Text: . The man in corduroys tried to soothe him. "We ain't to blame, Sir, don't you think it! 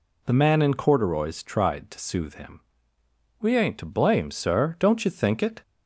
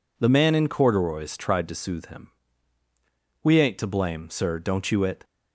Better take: first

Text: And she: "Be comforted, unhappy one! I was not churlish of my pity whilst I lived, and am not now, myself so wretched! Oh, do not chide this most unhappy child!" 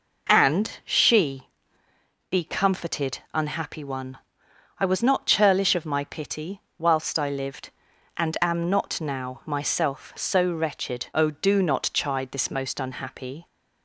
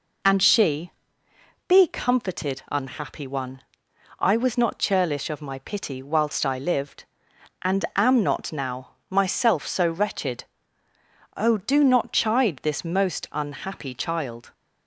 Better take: second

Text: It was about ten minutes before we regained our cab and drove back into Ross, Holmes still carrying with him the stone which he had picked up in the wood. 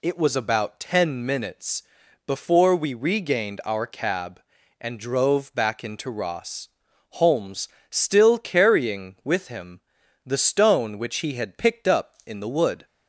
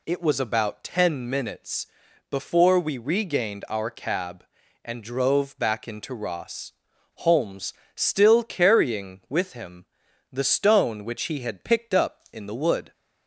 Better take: neither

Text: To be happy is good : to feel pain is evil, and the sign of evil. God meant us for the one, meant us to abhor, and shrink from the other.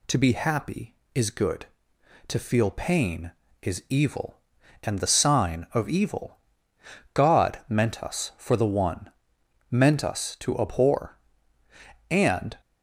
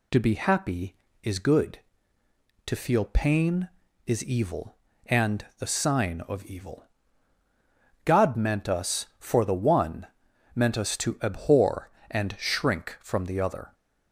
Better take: second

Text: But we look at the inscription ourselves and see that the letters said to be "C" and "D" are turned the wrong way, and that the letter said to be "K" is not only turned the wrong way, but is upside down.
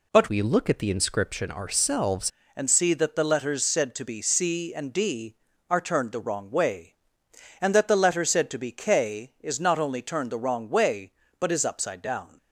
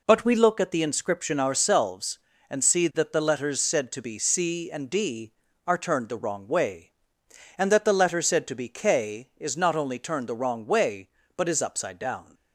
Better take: second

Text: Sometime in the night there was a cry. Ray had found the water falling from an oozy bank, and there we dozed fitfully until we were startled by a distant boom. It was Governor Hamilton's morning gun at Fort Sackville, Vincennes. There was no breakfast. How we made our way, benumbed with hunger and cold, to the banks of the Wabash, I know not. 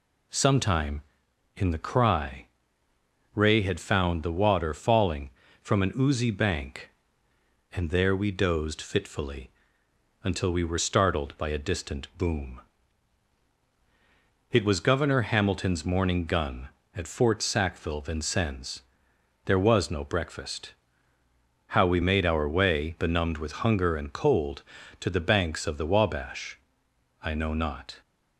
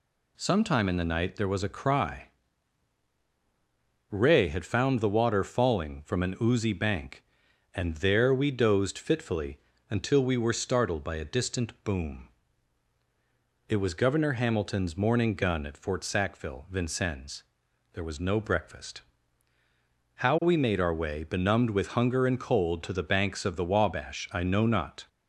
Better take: second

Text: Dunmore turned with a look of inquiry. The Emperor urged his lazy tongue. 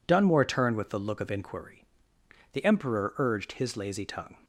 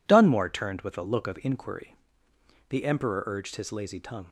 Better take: neither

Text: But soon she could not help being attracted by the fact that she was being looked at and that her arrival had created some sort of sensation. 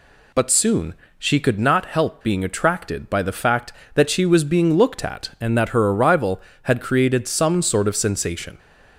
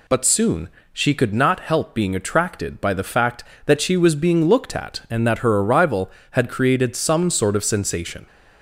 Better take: neither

